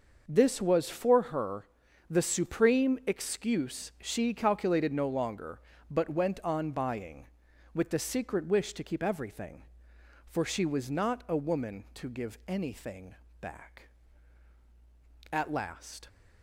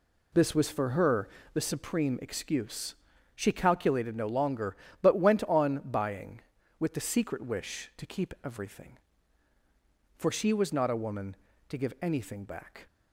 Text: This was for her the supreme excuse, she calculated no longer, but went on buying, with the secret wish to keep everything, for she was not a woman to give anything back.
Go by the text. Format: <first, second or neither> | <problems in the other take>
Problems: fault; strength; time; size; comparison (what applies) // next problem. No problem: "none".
second | starts louder than the rest; noticeable; until 1.2 s; 6 dB // pauses between "her" and "the"; at 1.6 s; 0.44 s long; slight in the second // pauses between "anything" and "back"; slight; at 13.1 s; 0.26 s long // goes on to say "At last"; noticeable; from 15.3 s on; 0.76 s long